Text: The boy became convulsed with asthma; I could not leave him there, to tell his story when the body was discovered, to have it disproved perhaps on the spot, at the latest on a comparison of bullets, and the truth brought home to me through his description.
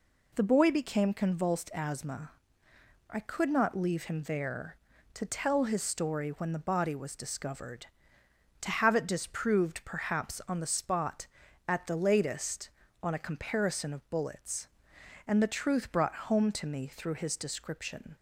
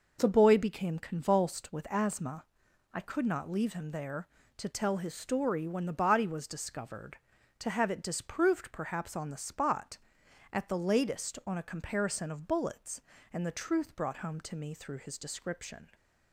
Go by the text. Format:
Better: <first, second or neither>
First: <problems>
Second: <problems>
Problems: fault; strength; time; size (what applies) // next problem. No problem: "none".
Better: second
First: skips "with"; at 1.7 s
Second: none